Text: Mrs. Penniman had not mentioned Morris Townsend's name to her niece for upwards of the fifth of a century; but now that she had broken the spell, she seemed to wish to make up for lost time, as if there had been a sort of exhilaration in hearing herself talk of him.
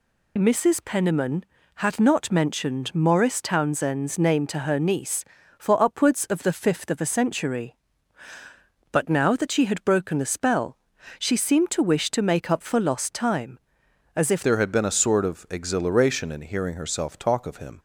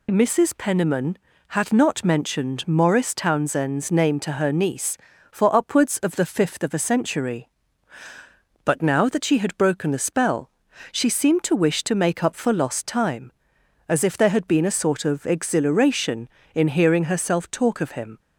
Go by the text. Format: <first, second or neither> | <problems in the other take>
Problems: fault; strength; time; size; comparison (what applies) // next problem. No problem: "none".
second | changes voice at "there"; from 14.4 s on; 3.3 s long